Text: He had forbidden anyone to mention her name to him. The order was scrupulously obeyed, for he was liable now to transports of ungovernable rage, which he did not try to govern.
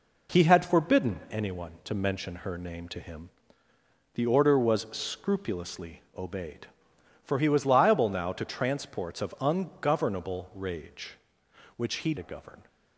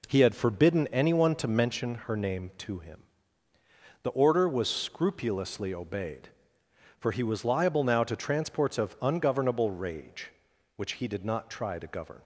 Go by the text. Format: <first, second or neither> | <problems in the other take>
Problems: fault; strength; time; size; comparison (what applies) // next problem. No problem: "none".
second | skips "did not try"; at 12.1 s